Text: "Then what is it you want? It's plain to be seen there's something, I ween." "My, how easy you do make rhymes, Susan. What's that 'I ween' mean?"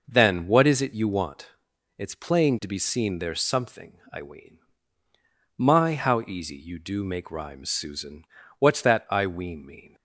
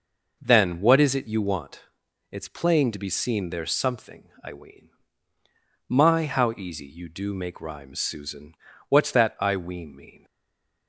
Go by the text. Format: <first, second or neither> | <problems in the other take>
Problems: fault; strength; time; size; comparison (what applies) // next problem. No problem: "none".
first | stays silent after the last word; slight; from 10.2 s on; 0.6 s long